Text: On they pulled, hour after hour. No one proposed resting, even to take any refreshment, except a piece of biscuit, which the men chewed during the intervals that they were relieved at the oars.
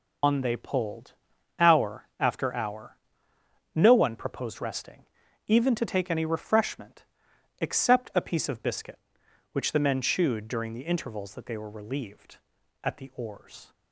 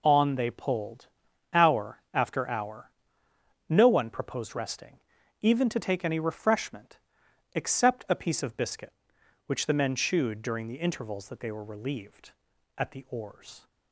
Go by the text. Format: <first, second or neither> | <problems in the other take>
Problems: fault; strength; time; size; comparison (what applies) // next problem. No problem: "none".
second | loses the start of "On"; at 0.2 s; 145 ms